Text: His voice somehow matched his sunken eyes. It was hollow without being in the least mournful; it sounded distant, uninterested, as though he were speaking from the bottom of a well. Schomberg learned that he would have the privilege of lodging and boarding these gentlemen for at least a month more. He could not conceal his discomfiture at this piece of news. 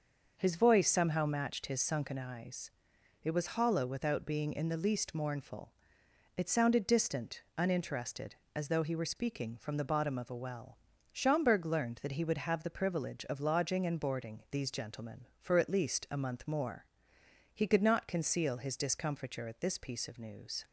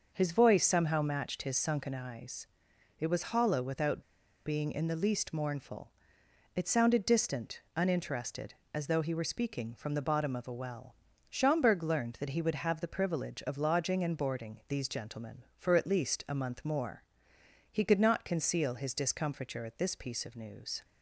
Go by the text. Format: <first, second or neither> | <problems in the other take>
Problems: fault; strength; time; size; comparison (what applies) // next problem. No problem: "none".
first | starts louder than the rest; until 1.1 s; 6.5 dB; also in the first // pauses between "without" and "being"; at 4.0 s; 0.44 s long